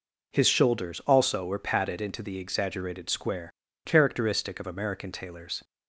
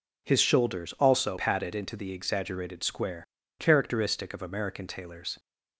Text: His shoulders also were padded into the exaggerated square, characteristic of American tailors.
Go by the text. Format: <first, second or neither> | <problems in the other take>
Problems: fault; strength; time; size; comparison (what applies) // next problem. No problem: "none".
first | skips "were"; at 1.3 s